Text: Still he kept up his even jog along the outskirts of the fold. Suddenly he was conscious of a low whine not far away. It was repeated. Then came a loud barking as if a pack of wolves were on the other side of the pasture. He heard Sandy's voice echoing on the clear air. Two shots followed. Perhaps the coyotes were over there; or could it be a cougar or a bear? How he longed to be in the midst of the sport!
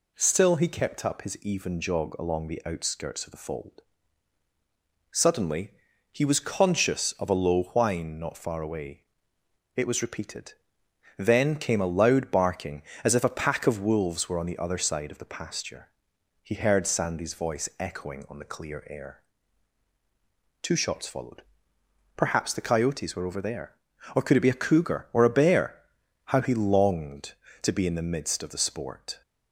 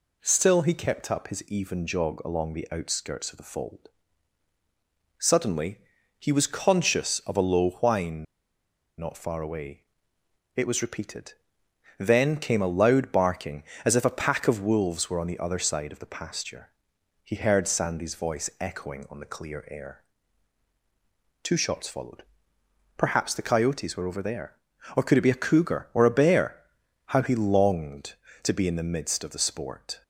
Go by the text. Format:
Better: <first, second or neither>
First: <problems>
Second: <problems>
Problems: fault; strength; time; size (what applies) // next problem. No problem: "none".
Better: first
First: pauses between "Suddenly" and "he"; at 5.7 s; 0.40 s long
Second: pauses between "Suddenly" and "he"; at 5.7 s; 0.40 s long // pauses between "whine" and "not"; noticeable; at 8.2 s; 0.73 s long